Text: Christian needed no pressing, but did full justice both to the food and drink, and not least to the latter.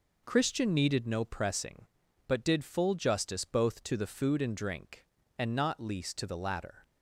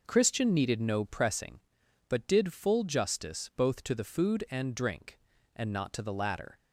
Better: first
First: none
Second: skips "least"; at 5.9 s

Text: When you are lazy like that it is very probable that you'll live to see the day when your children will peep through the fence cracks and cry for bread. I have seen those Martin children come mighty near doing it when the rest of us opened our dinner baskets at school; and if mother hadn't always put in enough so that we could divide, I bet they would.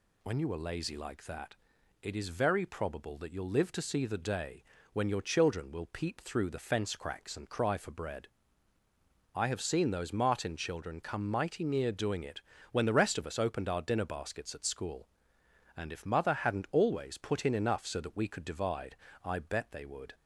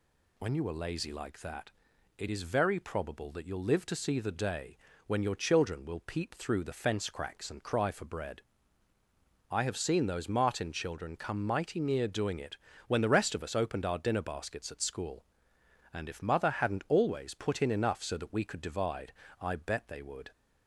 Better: neither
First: pauses between "that" and "it"; noticeable; at 1.5 s; 0.48 s long // pauses between "day" and "when"; slight; at 4.6 s; 0.30 s long // pauses between "it" and "when"; slight; at 12.4 s; 0.30 s long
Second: pauses between "that" and "it"; noticeable; at 1.7 s; 0.48 s long // pauses between "day" and "when"; slight; at 4.7 s; 0.30 s long // pauses between "it" and "when"; slight; at 12.5 s; 0.30 s long

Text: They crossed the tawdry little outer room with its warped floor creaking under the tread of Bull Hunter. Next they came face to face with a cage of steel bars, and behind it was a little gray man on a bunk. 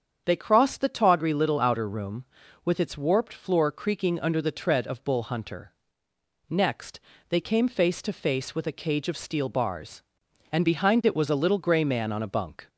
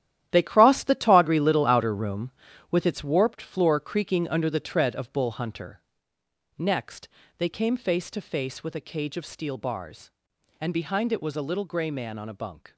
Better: first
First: starts louder than the rest; strong; until 1.2 s; 7.5 dB // pauses between "Next" and "they"; slight; at 7.0 s; 0.30 s long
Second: gets quieter; strong; throughout; 11.5 dB // starts louder than the rest; strong; until 1.3 s; 12 dB // pauses between "Next" and "they"; slight; at 7.0 s; 0.30 s long

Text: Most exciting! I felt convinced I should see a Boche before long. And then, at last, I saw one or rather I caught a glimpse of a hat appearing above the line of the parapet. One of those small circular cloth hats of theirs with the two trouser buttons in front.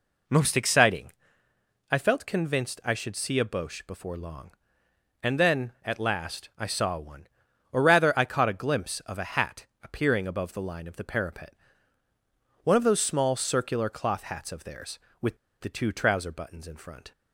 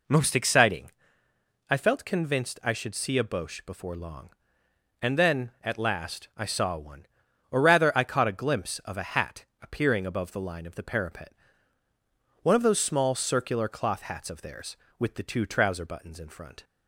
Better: second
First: pauses between "hat" and "appearing"; slight; at 9.6 s; 0.18 s long // pauses between "with" and "the"; slight; at 15.3 s; 0.25 s long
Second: pauses between "hat" and "appearing"; slight; at 9.4 s; 0.18 s long

